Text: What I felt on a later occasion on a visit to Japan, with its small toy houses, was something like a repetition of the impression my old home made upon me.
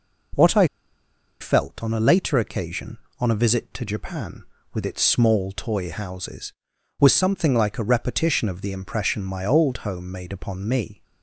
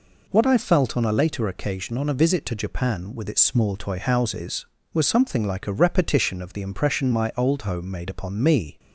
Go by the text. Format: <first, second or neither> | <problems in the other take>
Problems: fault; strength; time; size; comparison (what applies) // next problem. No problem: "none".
second | pauses between "I" and "felt"; noticeable; at 0.6 s; 0.74 s long